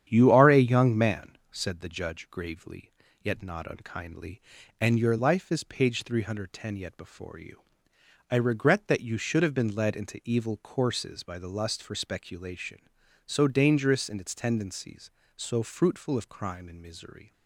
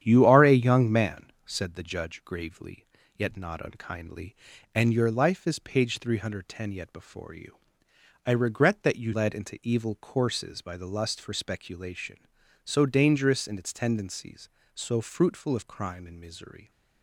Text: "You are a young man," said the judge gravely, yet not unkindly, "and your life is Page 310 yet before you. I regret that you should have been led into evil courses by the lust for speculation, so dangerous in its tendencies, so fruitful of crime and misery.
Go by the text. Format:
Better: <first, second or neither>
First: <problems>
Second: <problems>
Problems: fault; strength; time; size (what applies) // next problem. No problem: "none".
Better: first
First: starts louder than the rest; strong; until 1.0 s; 9.5 dB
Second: starts louder than the rest; strong; until 1.0 s; 9.5 dB // skips "should have been"; at 9.1 s